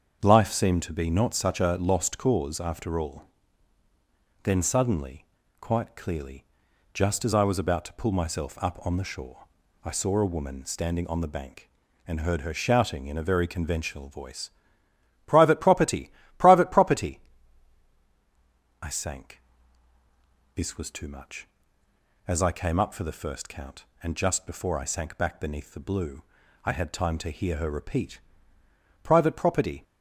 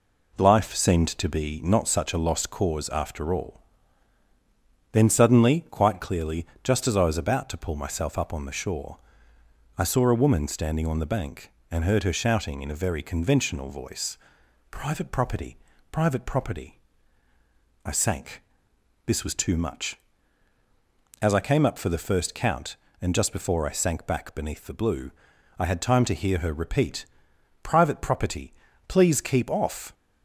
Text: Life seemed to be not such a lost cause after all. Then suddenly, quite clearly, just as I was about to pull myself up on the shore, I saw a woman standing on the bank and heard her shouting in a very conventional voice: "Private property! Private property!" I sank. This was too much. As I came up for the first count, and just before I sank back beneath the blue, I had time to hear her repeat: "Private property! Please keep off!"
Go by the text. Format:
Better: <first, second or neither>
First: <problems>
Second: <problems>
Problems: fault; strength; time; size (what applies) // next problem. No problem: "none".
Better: second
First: starts louder than the rest; until 1.2 s; 7 dB // stops before "Please keep off"; at 29.8 s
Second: none